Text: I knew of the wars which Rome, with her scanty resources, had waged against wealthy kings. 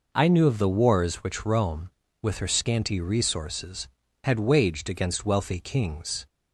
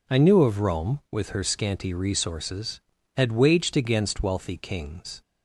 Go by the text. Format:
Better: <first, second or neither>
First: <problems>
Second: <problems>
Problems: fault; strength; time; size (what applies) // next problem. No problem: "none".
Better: first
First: none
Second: skips "the wars which"; at 0.6 s